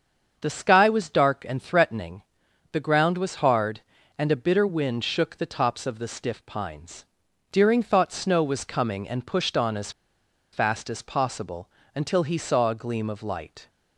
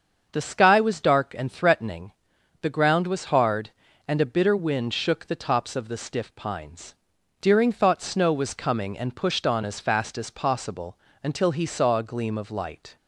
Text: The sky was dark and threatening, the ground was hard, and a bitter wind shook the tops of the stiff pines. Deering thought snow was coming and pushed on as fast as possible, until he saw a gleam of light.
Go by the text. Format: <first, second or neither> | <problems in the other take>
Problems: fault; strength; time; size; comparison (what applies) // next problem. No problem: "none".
second | starts louder than the rest; until 1.4 s; 7 dB; also in the second // pauses between "as" and "fast"; noticeable; at 9.8 s; 0.62 s long